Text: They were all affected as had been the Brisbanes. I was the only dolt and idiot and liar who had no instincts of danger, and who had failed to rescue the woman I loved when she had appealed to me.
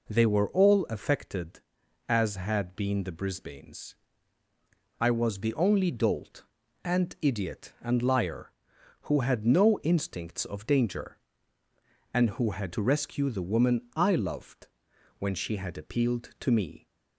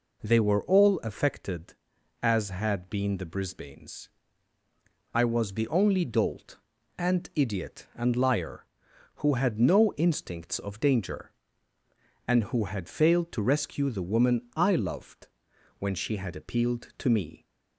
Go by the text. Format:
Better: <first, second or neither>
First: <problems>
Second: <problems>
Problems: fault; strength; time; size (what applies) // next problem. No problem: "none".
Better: second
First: skips "failed"; at 12.7 s // pauses between "loved" and "when"; noticeable; at 14.6 s; 0.50 s long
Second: pauses between "loved" and "when"; noticeable; at 15.2 s; 0.50 s long